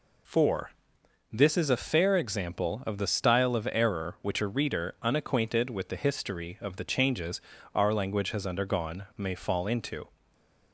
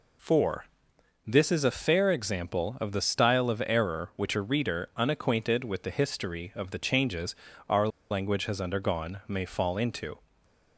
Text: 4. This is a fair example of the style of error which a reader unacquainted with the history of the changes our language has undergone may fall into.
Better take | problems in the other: first | pauses between "changes" and "our"; slight; at 7.3 s; 0.36 s long; slight in the first // pauses between "our" and "language"; slight; at 7.8 s; 0.22 s long // stays silent after the last word; slight; from 10.1 s on; 0.6 s long; slight in the first

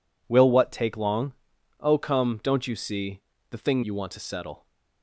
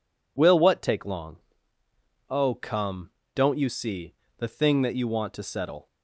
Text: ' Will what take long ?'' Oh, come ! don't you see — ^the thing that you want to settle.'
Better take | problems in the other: second | skips "that"; at 3.8 s

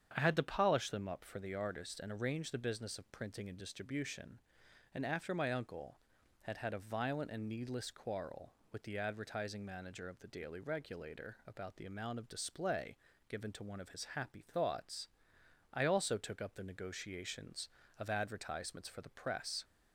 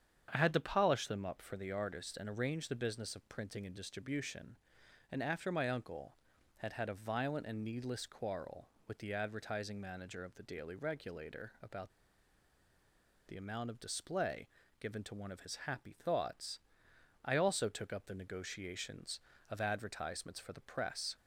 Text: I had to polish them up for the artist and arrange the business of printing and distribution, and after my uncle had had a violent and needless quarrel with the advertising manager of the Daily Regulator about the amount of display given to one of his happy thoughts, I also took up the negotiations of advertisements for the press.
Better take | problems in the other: first | starts louder than the rest; strong; until 1.3 s; 8.5 dB; strong in the first // pauses between "about" and "the"; strong; at 11.9 s; 1.3 s long // pauses between "display" and "given"; slight; at 14.4 s; 0.32 s long; slight in the first

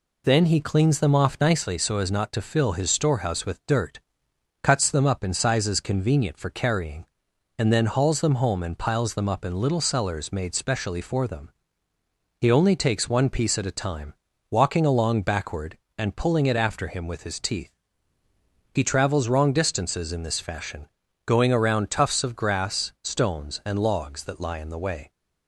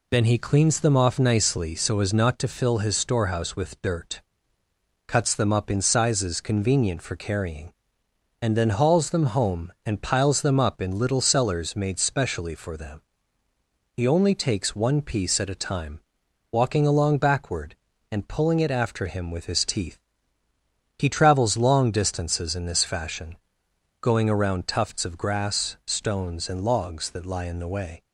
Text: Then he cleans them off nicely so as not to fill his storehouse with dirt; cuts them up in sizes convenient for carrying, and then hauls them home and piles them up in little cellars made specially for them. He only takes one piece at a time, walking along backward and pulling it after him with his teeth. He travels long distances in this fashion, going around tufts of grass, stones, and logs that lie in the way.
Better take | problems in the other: second | says "wrong" for "long"; at 19.2 s

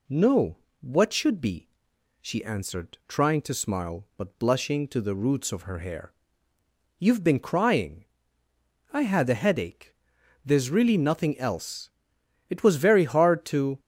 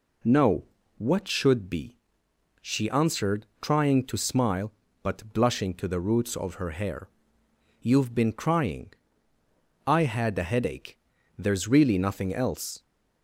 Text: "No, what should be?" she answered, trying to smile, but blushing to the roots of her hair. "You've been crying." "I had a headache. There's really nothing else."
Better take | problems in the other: second | goes on to say "It was very hard to"; noticeable; from 12.4 s on; 1.3 s long

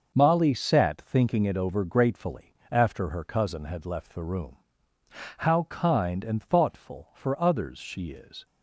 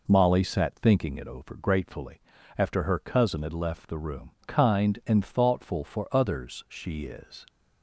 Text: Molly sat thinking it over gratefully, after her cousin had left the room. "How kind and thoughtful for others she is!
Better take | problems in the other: first | skips "How"; at 4.3 s

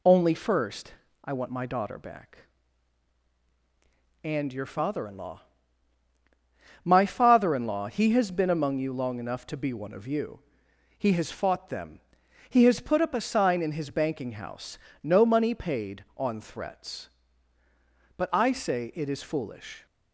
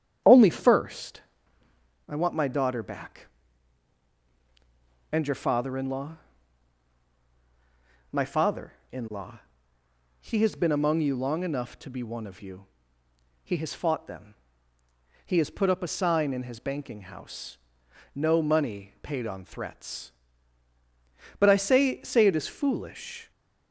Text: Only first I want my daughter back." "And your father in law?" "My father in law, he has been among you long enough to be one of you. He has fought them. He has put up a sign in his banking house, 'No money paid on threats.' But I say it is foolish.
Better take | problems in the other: first | starts louder than the rest; strong; until 2.1 s; 9 dB // pauses between "first" and "I"; noticeable; at 1.2 s; 0.88 s long; slight in the first // says "say" twice; at 22.0 s

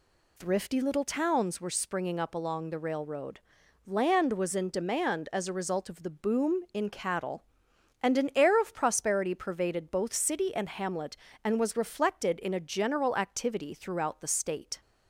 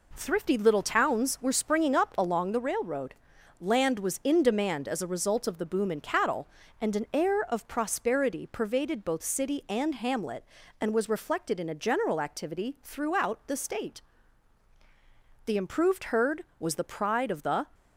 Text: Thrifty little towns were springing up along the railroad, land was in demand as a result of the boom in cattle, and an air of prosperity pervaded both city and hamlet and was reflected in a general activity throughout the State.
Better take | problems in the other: first | goes on to say "The improved herd was the pride of the"; strong; from 15.4 s on; 2.2 s long

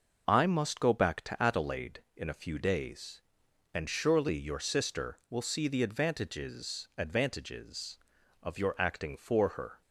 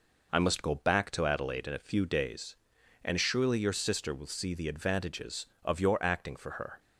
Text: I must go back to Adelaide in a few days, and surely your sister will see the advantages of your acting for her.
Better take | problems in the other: second | says "advantages" twice; at 6.9 s

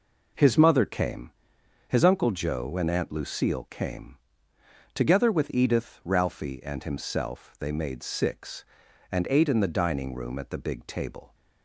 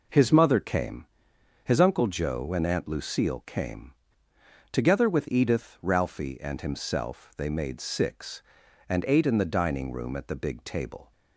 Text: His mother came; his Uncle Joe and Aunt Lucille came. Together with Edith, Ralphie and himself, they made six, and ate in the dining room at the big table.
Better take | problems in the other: neither | none

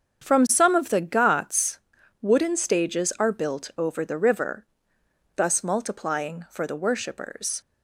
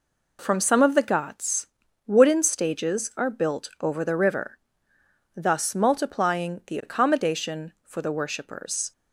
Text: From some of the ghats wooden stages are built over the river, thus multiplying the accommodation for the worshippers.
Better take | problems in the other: second | starts louder than the rest; strong; until 1.2 s; 7.5 dB // pauses between "ghats" and "wooden"; at 1.8 s; 0.42 s long; also in the second // skips "the accommodation"; at 6.4 s

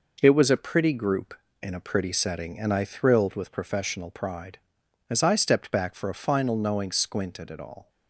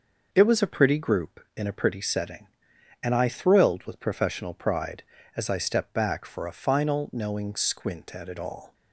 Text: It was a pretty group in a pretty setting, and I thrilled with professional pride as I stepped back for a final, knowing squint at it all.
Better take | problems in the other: second | gets quieter; noticeable; throughout; 6 dB

